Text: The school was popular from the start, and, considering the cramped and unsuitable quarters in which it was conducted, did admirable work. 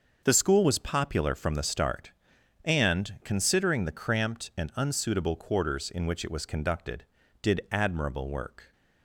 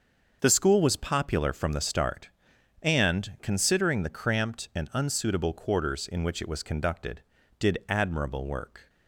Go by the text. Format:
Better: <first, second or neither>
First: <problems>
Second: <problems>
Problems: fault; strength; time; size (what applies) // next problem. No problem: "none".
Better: neither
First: starts louder than the rest; until 1.2 s; 6.5 dB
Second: starts louder than the rest; until 1.4 s; 6.5 dB